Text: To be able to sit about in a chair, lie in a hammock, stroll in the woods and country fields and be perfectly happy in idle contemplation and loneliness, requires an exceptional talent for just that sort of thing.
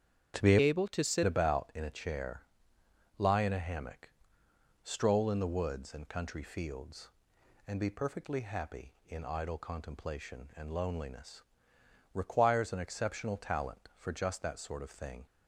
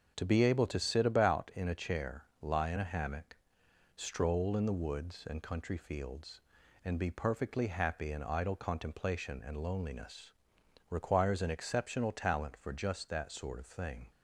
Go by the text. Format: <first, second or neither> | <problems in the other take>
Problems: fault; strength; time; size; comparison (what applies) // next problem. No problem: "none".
second | starts louder than the rest; strong; until 1.4 s; 8.5 dB; also in the second // changes voice from "able" to "sit"; from 0.6 to 1.2 s; 0.6 s long